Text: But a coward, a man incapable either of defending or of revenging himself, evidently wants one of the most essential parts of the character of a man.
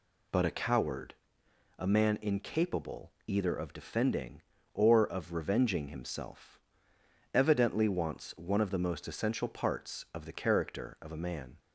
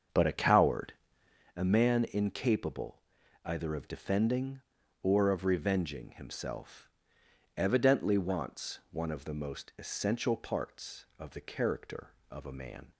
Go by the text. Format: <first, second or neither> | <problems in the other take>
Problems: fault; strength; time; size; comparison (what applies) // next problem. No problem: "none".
first | starts louder than the rest; until 1.5 s; 7 dB // pauses between "incapable" and "either"; at 3.0 s; 0.42 s long